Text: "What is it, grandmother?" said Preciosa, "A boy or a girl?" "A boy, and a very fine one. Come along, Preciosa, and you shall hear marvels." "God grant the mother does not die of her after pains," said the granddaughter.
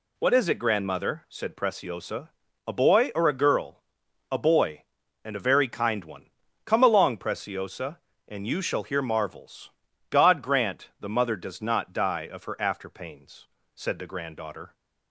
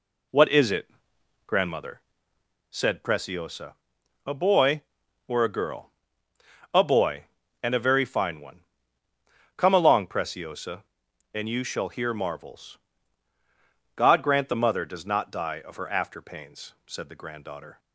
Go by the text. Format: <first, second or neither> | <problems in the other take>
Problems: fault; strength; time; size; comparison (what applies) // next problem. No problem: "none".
second | says "kind" for "fine"; at 5.6 s